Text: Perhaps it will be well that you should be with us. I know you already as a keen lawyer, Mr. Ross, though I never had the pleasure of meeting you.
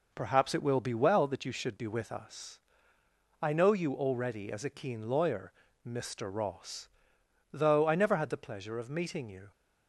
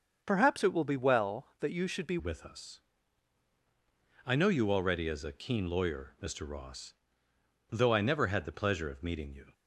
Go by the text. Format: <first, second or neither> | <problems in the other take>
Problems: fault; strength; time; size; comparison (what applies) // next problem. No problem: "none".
first | starts louder than the rest; until 1.2 s; 6.5 dB // changes voice at "with"; from 2.1 s on; 7.4 s long